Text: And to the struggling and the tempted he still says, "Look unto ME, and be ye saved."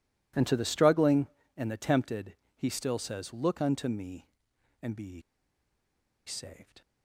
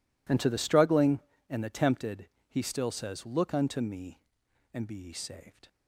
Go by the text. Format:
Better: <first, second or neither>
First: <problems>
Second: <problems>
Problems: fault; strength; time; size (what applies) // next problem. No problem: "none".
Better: second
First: pauses between "tempted" and "he"; slight; at 2.3 s; 0.22 s long // pauses between "ye" and "saved"; at 5.2 s; 1.0 s long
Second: pauses between "tempted" and "he"; slight; at 2.2 s; 0.22 s long